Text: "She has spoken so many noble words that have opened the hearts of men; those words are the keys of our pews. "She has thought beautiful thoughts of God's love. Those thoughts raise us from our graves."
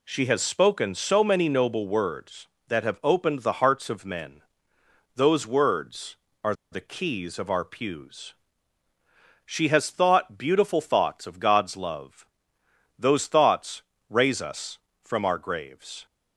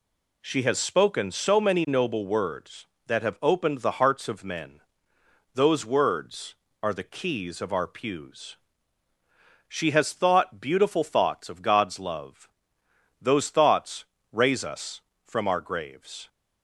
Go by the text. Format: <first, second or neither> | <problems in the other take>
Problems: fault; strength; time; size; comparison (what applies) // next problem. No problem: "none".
second | pauses between "are" and "the"; slight; at 6.5 s; 0.18 s long // pauses between "thoughts" and "raise"; slight; at 13.8 s; 0.28 s long; slight in the second